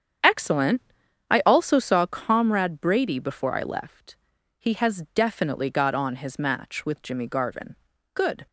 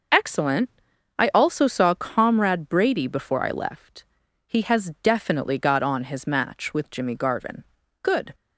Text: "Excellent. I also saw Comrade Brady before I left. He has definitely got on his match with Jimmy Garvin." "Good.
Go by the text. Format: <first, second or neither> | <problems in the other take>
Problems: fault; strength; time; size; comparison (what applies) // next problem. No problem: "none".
second | starts louder than the rest; strong; until 2.0 s; 8 dB